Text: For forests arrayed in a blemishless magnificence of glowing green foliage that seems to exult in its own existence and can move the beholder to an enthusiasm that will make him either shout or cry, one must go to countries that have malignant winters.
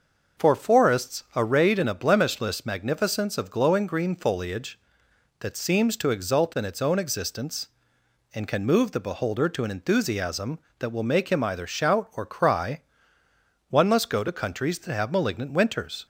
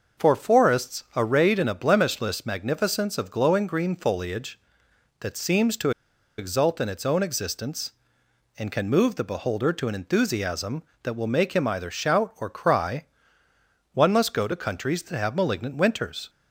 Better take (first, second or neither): first